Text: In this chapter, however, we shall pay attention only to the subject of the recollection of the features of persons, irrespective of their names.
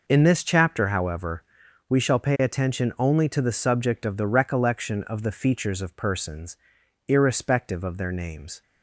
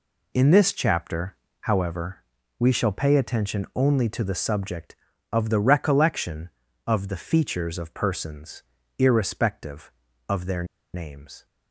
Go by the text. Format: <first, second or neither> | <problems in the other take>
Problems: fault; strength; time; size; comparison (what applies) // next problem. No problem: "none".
first | pauses between "their" and "names"; slight; at 10.6 s; 0.29 s long